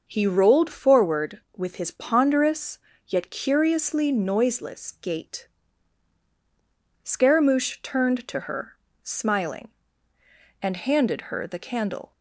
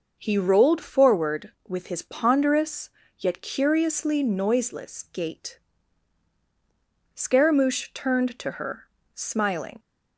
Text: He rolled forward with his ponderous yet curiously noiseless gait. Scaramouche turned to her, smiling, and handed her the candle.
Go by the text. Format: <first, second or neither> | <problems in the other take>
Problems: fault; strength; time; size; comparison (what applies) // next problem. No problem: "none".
first | pauses between "ponderous" and "yet"; slight; at 2.8 s; 0.30 s long; slight in the first // stops before "and handed her the candle"; at 9.7 s